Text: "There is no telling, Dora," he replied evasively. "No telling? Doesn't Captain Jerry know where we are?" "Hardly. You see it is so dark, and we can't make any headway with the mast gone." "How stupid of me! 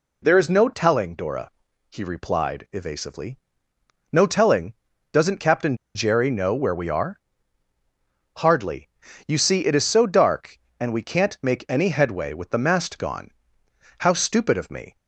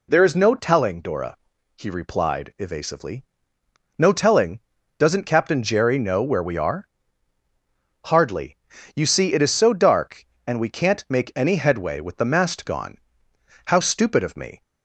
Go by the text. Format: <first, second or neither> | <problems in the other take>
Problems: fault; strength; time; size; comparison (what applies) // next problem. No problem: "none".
second | pauses between "Captain" and "Jerry"; slight; at 5.7 s; 0.19 s long